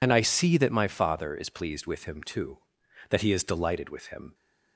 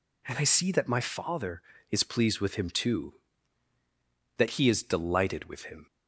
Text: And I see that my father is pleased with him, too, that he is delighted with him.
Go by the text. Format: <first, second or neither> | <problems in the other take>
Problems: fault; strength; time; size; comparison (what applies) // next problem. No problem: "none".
second | loses the start of "And"; at 0.0 s; 40 ms